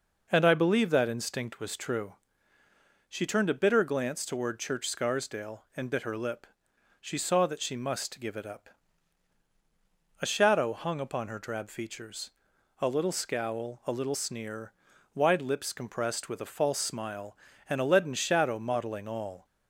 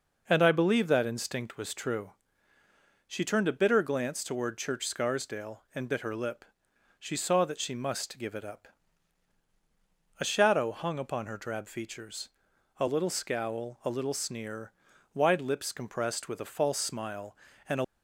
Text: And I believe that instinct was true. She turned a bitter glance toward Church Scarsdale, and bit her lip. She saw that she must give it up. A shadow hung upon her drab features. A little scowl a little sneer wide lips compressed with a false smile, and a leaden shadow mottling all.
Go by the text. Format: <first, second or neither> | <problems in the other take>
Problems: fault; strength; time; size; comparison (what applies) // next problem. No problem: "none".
first | pauses between "sneer" and "wide"; at 14.7 s; 0.42 s long; also in the first // stops before "leaden shadow mottling all"; at 17.8 s